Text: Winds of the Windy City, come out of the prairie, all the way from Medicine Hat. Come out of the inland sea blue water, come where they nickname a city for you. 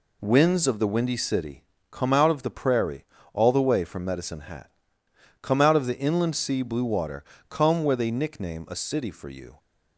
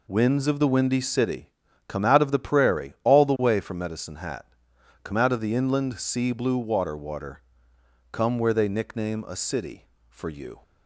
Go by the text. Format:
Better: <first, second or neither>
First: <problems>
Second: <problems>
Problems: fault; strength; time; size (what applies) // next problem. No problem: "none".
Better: first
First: none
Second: says "water" twice; at 6.9 s